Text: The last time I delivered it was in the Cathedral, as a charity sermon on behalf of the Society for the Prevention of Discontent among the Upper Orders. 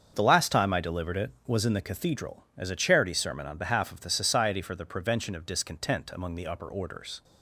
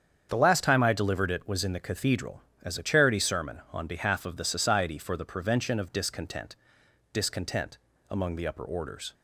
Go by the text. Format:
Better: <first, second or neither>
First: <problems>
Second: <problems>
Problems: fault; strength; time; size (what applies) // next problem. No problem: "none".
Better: first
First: starts louder than the rest; strong; until 1.1 s; 7 dB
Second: starts louder than the rest; strong; until 1.3 s; 8 dB // says "Discontent" twice; at 7.1 s